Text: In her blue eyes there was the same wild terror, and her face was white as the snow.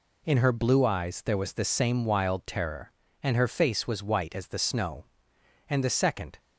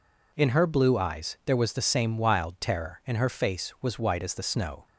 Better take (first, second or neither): second